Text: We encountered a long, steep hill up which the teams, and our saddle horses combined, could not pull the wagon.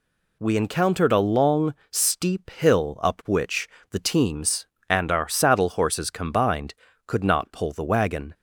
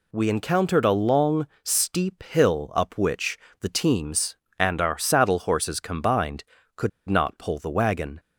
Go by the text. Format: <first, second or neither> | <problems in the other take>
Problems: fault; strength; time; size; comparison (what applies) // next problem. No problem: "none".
first | pauses between "which" and "the"; slight; at 3.3 s; 0.24 s long; slight in the first // pauses between "could" and "not"; slight; at 6.8 s; 0.19 s long